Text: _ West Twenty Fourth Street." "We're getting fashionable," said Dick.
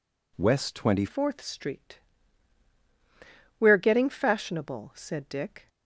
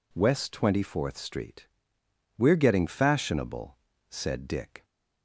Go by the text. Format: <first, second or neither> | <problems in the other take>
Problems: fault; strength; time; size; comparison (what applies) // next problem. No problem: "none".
second | changes voice at "Fourth"; from 1.0 s on; 4.6 s long